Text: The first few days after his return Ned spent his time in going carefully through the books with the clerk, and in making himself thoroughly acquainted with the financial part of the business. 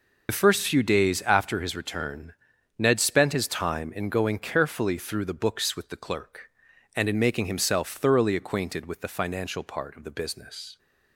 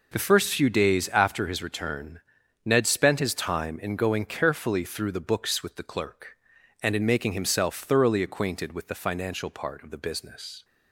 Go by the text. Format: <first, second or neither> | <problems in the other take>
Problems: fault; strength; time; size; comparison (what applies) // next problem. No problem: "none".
second | loses the start of "The"; at 0.2 s; 45 ms // pauses between "return" and "Ned"; noticeable; at 2.3 s; 0.46 s long; noticeable in the second